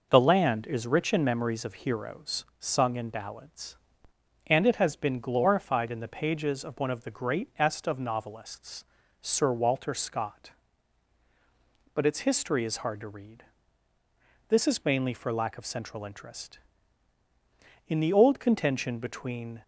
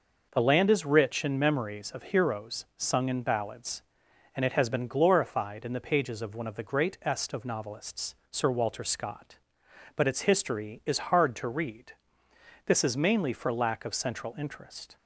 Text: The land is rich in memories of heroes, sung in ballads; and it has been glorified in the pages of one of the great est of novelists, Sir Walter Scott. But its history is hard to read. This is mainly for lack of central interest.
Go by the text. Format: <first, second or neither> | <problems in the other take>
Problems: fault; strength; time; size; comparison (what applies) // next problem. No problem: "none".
second | goes on to say "In the old contention between"; strong; from 17.8 s on; 1.7 s long